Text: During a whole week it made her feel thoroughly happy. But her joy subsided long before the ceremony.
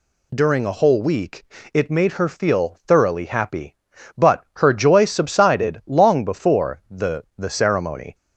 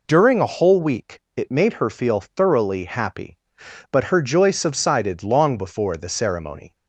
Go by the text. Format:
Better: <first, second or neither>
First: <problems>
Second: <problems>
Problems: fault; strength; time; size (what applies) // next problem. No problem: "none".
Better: second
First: pauses between "week" and "it"; slight; at 1.4 s; 0.28 s long // says "the" twice; at 7.3 s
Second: pauses between "week" and "it"; slight; at 1.1 s; 0.16 s long